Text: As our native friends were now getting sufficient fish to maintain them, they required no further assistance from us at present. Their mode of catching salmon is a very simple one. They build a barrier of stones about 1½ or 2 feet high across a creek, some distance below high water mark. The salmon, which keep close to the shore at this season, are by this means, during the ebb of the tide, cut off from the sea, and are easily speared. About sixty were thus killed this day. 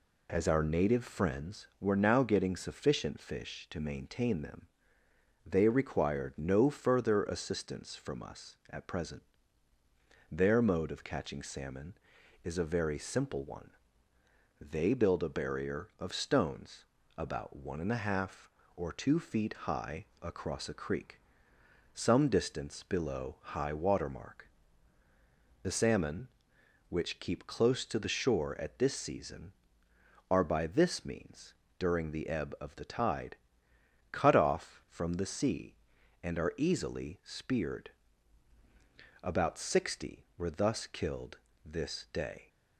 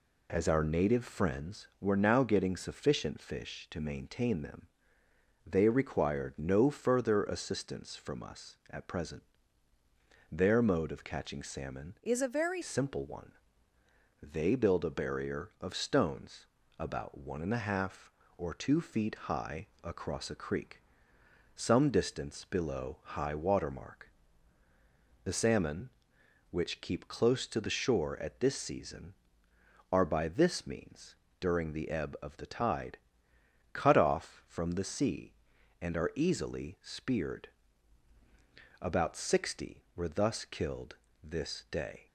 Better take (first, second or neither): first